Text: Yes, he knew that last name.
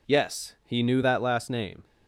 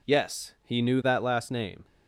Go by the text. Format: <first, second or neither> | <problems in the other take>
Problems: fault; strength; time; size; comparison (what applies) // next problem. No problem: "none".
neither | none